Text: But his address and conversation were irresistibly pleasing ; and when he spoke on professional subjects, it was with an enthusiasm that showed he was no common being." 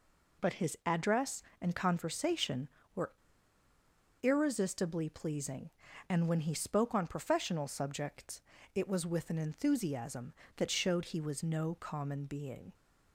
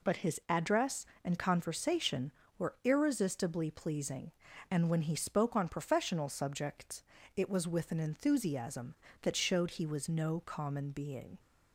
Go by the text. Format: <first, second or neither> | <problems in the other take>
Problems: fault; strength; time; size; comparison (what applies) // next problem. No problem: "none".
second | pauses between "were" and "irresistibly"; at 3.1 s; 1.0 s long